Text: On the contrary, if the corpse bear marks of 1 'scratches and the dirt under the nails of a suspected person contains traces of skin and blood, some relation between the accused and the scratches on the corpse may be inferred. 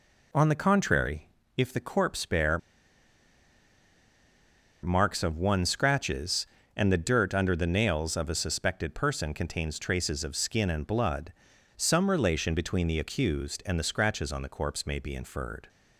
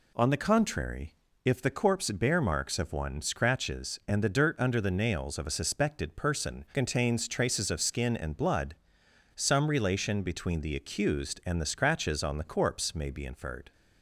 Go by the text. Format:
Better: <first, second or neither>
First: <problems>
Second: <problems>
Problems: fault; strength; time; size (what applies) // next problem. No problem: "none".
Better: second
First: pauses between "bear" and "marks"; strong; at 2.5 s; 2.2 s long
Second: none